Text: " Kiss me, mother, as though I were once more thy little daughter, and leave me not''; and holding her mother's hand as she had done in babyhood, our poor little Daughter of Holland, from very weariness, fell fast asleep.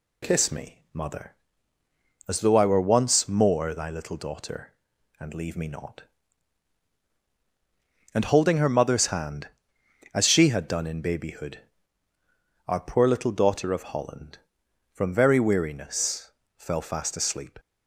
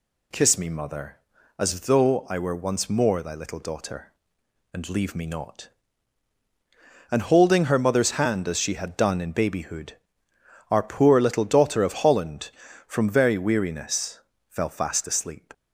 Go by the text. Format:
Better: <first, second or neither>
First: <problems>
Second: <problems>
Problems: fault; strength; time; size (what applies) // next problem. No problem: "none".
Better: neither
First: none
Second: none